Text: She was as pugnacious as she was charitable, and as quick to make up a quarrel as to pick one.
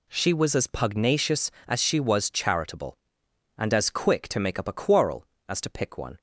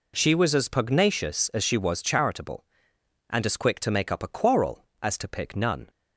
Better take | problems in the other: first | says "none" for "one"; at 5.5 s

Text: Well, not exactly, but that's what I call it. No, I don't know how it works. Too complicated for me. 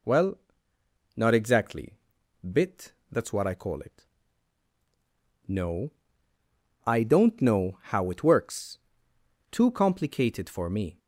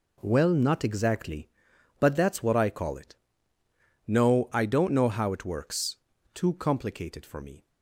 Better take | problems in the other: second | says "bit" for "but"; at 2.4 s

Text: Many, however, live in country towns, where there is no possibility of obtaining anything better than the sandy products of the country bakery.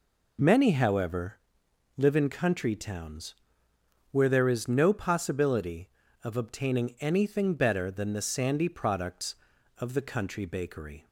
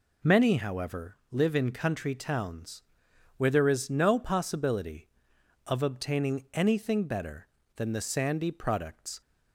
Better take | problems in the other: first | stops before "of the country bakery"; at 9.2 s

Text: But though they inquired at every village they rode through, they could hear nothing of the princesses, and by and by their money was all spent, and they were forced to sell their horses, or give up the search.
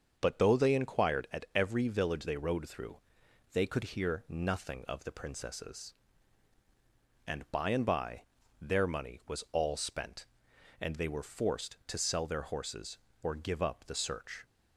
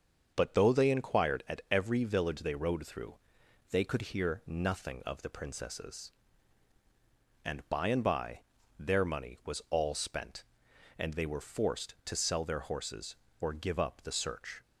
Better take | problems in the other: neither | starts louder than the rest; the same in both // pauses between "by" and "their"; the same in both

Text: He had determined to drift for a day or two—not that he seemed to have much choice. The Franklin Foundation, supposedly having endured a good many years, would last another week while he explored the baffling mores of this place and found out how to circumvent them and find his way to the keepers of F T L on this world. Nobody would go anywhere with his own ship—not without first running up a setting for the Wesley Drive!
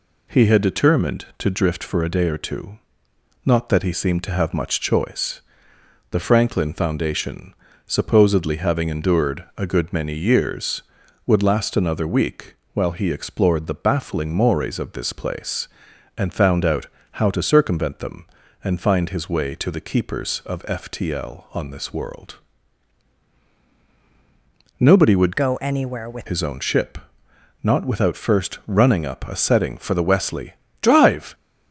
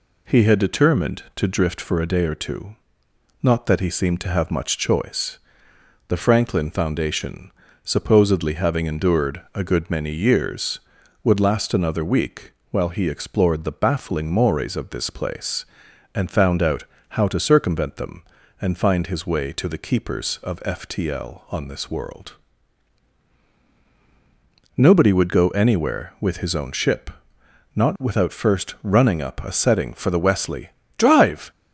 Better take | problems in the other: second | pauses between "week" and "while"; slight; at 12.5 s; 0.20 s long; slight in the second // pauses between "out" and "how"; slight; at 16.8 s; 0.28 s long; slight in the second // changes voice from "go" to "with"; from 25.3 to 26.2 s; 0.9 s long // pauses between "Wesley" and "Drive"; slight; at 30.5 s; 0.30 s long; slight in the second

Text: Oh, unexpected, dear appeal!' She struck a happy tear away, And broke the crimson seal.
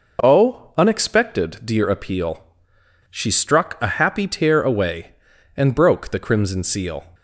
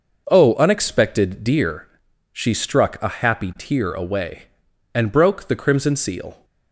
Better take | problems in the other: first | skips "appeal"; at 2.0 s

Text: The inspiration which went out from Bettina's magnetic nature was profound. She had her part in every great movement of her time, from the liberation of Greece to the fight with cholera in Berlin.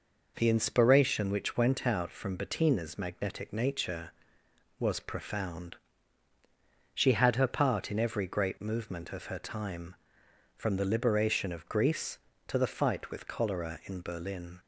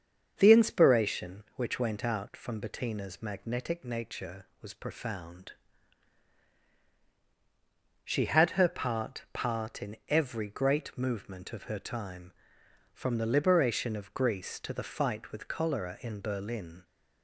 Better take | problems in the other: first | starts louder than the rest; until 1.3 s; 7 dB // says "part" twice; at 9.3 s

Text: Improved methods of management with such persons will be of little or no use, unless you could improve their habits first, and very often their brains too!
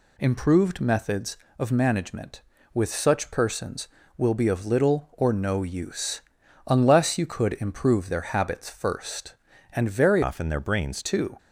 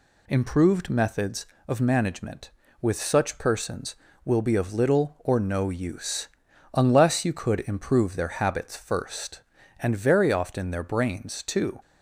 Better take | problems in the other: second | changes voice from "often" to "brains"; from 10.2 to 11.0 s; 0.8 s long

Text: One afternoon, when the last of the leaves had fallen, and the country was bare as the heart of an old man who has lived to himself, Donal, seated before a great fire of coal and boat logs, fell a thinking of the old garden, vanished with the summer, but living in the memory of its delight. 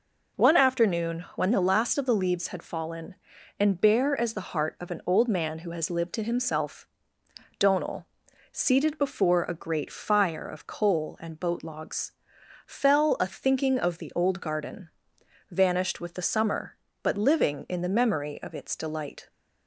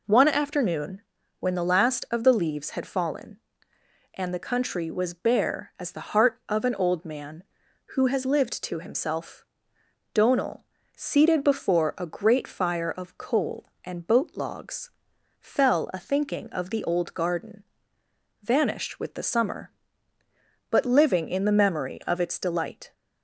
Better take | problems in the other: second | skips "the country was"; at 3.8 s

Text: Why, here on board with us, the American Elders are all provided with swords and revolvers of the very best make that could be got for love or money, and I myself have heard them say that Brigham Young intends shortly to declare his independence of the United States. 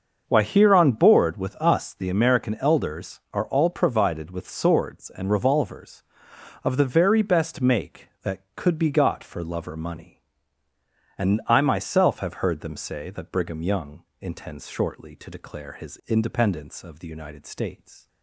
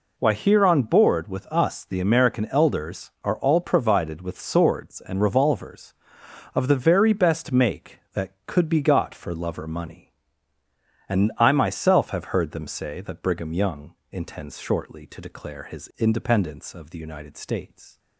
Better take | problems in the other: second | starts louder than the rest; until 1.9 s; 6 dB // pauses between "Young" and "intends"; slight; at 14.0 s; 0.18 s long; slight in the second

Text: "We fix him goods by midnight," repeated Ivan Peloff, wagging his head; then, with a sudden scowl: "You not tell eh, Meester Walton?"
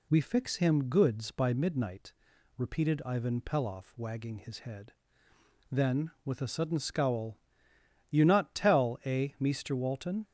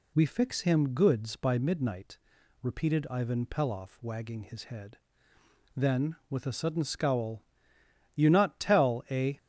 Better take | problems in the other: first | stops before "Meester Walton"; at 9.3 s

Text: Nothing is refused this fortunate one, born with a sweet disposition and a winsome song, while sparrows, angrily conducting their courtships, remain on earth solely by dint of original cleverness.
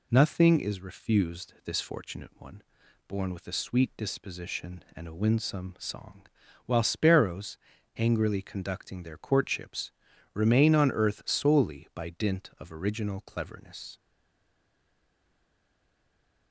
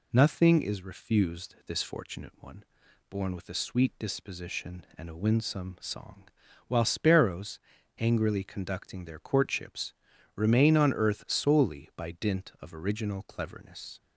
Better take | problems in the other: second | stays silent after the last word; strong; from 13.9 s on; 2.6 s long

